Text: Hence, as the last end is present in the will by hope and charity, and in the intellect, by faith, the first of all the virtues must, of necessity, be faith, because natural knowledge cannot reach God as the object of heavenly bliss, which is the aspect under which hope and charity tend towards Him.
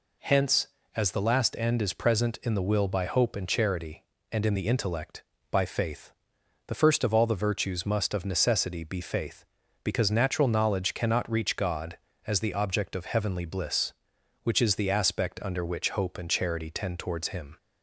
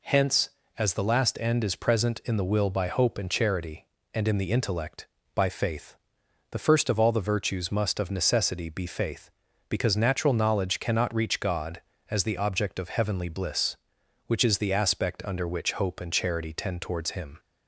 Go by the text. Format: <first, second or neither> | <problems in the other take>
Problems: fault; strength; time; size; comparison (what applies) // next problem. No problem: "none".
neither | none